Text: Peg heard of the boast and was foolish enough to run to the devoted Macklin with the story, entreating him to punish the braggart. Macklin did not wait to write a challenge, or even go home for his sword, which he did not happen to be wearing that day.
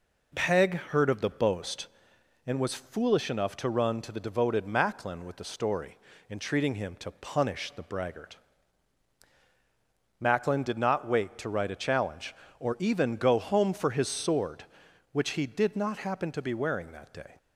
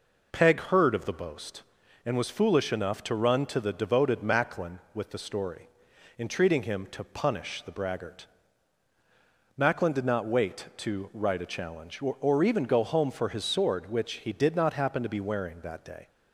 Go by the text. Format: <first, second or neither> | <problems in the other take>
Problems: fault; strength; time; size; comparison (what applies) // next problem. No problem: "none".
first | says "or" twice; at 12.2 s